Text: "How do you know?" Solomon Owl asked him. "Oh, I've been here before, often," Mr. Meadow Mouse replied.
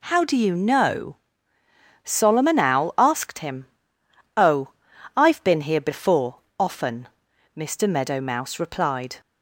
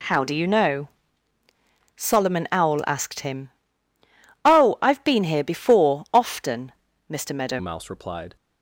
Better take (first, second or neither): first